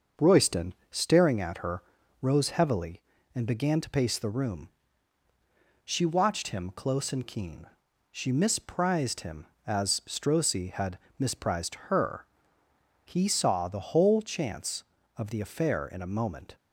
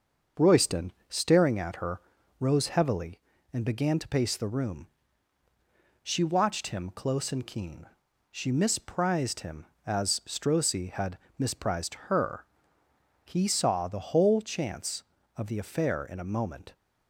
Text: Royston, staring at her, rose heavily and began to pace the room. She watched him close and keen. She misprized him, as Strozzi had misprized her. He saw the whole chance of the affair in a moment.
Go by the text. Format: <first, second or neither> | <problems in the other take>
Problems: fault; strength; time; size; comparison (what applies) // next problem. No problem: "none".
neither | starts louder than the rest; the same in both // pauses between "had" and "misprized"; slight; the same in both